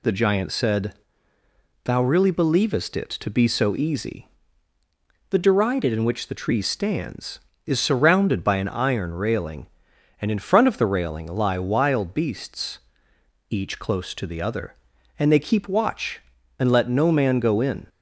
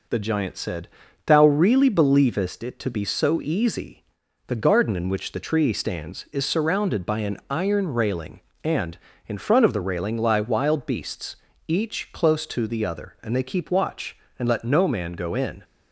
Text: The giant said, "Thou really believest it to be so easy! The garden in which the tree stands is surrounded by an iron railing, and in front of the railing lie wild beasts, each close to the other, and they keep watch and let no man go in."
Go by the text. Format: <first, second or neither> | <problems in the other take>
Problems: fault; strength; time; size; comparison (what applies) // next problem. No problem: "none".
second | says "derided" for "garden"; at 5.3 s